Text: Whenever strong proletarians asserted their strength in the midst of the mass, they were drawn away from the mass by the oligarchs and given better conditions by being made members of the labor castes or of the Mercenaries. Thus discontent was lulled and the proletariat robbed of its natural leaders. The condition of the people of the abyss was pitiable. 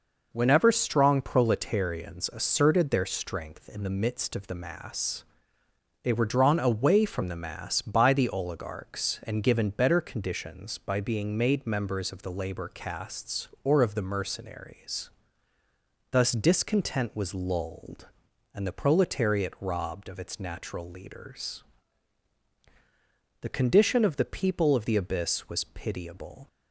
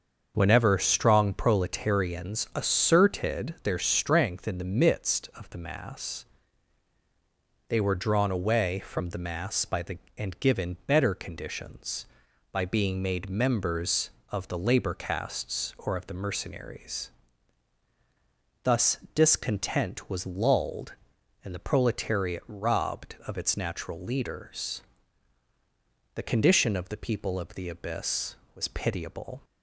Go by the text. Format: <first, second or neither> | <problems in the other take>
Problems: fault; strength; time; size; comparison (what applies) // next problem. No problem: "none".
first | starts louder than the rest; until 1.3 s; 6.5 dB // skips "oligarchs"; at 10.0 s // pauses between "Thus" and "discontent"; slight; at 18.9 s; 0.16 s long